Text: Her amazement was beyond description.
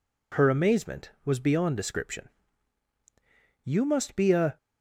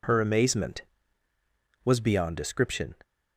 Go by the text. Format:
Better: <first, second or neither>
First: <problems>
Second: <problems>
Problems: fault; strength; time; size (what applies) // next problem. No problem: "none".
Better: second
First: goes on to say "You must be a"; noticeable; from 3.6 s on; 0.96 s long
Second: none